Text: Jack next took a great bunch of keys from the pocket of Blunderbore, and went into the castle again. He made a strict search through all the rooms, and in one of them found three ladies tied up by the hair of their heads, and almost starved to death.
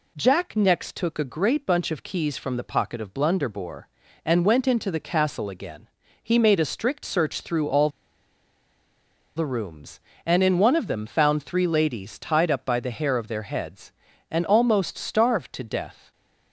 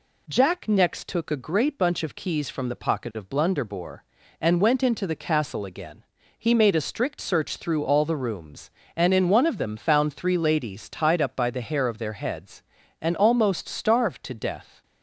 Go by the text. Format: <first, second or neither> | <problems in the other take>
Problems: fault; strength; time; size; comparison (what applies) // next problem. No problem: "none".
second | pauses between "all" and "the"; strong; at 7.8 s; 1.4 s long